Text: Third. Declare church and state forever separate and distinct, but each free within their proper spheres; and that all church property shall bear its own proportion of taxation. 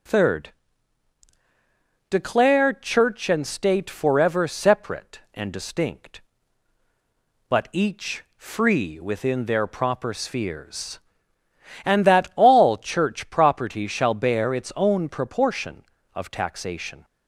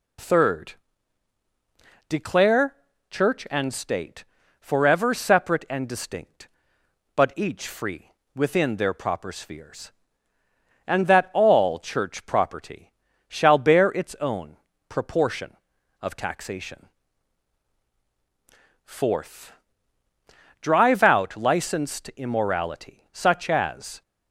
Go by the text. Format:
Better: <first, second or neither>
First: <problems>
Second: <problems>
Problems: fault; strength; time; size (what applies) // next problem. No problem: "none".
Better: first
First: none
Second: pauses between "Declare" and "church"; slight; at 2.7 s; 0.34 s long // pauses between "state" and "forever"; slight; at 4.2 s; 0.36 s long // pauses between "free" and "within"; slight; at 8.1 s; 0.24 s long // pauses between "property" and "shall"; slight; at 12.9 s; 0.36 s long // pauses between "own" and "proportion"; slight; at 14.5 s; 0.32 s long // goes on to say "Fourth Drive out licensed immorality such as"; strong; from 18.8 s on; 5.1 s long